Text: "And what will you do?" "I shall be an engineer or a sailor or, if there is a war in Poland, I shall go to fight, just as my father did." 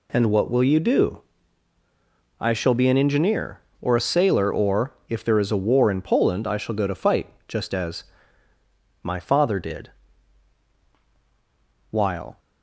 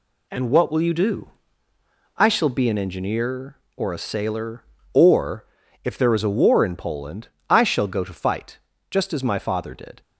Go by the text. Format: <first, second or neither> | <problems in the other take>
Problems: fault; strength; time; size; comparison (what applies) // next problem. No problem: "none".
second | pauses between "as" and "my"; at 8.0 s; 1.0 s long // goes on to say "While"; slight; from 11.9 s on; 0.48 s long